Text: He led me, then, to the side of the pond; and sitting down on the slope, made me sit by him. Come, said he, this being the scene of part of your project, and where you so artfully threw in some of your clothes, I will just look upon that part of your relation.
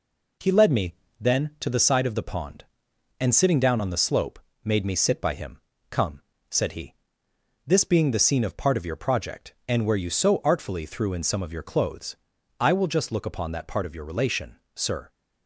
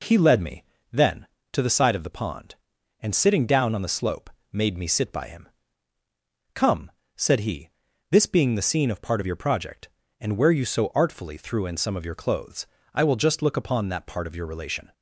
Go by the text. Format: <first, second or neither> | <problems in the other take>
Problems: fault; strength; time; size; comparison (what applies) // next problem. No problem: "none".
second | goes on to say "Sir"; slight; from 14.7 s on; 0.34 s long